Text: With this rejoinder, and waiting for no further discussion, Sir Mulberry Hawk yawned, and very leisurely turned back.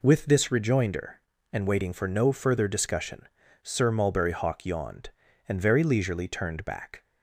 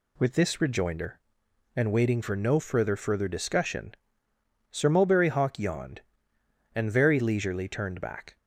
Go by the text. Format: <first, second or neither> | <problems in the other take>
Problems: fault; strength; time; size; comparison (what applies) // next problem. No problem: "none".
first | says "further" twice; at 2.9 s